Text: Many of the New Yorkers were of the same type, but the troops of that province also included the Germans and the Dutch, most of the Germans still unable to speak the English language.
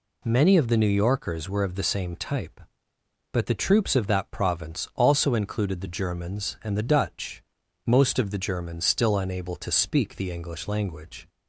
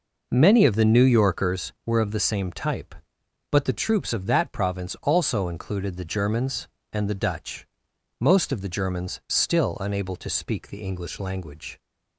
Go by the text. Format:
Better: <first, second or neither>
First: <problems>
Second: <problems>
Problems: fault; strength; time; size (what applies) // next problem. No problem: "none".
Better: first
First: none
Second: starts louder than the rest; noticeable; until 1.9 s; 5 dB